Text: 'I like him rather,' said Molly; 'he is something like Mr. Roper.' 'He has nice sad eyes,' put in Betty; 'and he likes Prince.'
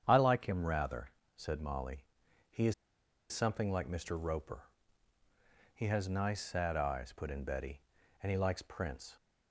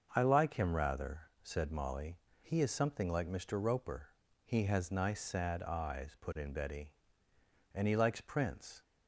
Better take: second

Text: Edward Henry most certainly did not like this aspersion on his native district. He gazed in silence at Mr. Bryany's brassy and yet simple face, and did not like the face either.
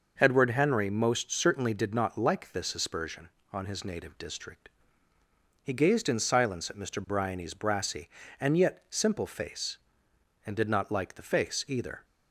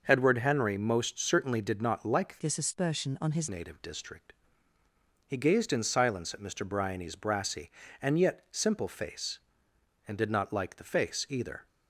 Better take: first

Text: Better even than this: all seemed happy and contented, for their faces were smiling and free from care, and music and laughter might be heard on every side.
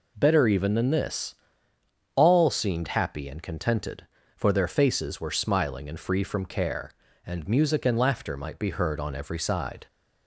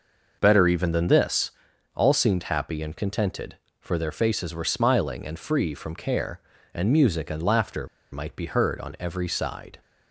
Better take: first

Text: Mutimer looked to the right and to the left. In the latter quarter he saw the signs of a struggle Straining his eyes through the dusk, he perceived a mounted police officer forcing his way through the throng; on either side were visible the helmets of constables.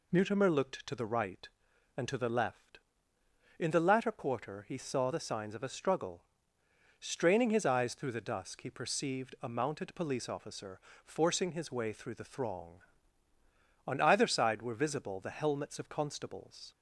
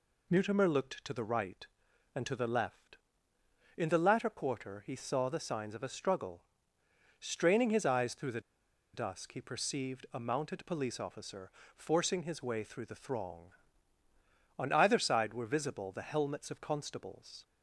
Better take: first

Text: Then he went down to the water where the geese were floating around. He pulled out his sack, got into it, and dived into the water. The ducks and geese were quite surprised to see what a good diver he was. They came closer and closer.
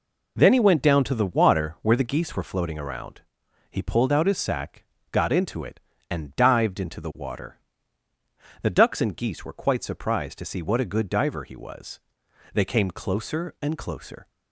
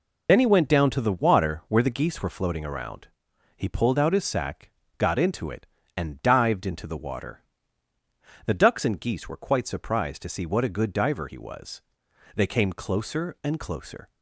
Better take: first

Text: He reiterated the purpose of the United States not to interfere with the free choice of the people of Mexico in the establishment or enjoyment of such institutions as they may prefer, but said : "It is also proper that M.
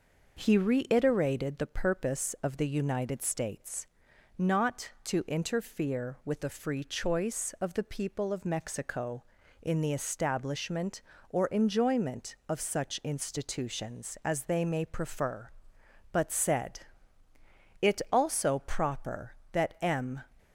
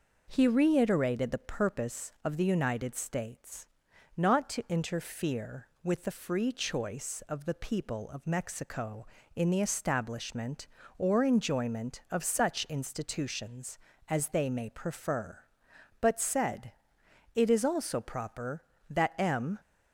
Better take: second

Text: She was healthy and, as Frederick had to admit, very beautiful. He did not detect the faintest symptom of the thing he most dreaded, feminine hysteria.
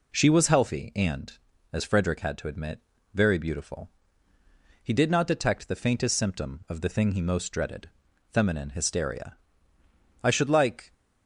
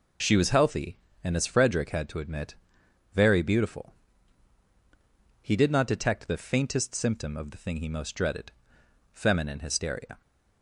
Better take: second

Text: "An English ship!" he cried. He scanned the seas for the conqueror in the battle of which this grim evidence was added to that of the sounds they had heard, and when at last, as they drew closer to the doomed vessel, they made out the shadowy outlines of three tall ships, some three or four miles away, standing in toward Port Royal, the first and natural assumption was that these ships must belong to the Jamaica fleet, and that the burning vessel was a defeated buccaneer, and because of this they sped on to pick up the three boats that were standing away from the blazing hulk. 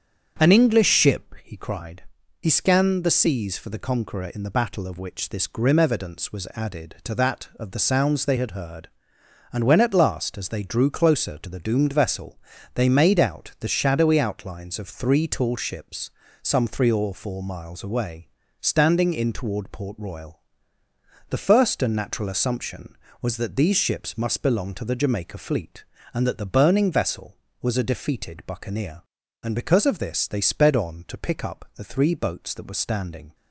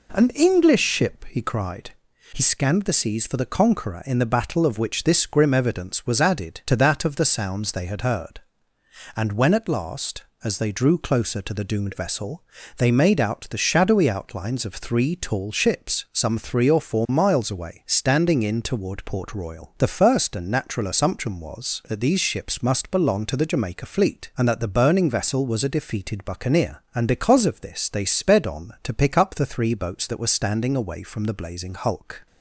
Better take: second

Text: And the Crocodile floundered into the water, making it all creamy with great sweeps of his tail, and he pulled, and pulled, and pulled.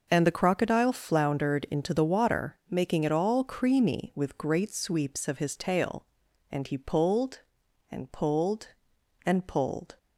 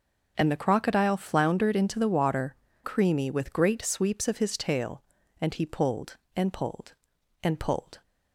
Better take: first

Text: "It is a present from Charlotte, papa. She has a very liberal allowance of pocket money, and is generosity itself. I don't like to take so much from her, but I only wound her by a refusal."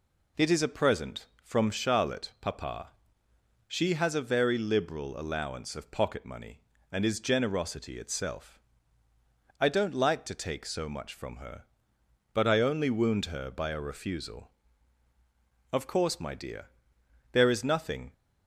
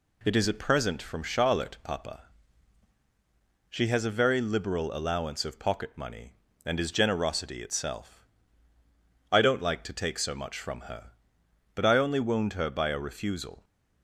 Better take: second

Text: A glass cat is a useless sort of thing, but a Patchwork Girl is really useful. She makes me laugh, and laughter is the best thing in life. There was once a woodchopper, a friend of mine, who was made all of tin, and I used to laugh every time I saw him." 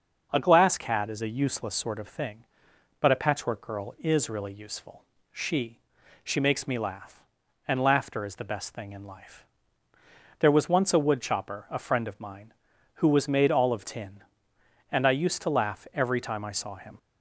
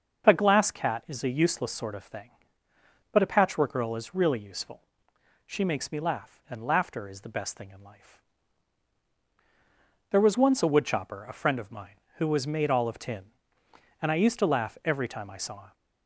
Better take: second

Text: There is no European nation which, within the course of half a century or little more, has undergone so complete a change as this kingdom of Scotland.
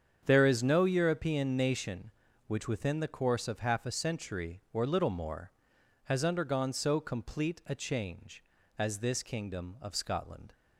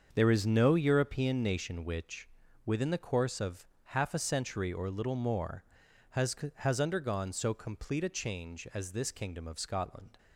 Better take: first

